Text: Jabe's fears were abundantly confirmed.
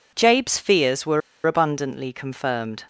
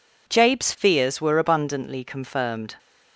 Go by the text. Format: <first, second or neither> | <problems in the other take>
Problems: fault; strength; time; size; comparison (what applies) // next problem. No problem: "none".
second | pauses between "were" and "abundantly"; slight; at 1.2 s; 0.26 s long